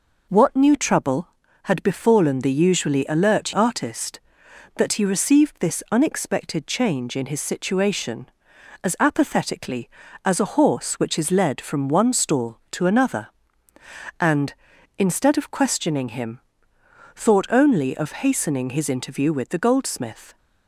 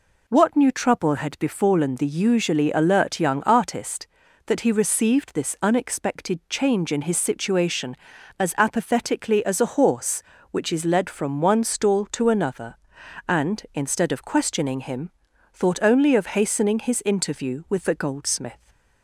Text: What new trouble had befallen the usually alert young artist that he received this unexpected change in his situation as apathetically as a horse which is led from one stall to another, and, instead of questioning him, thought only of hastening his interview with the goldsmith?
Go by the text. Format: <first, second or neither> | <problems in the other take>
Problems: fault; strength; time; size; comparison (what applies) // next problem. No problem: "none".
second | skips "young"; at 3.5 s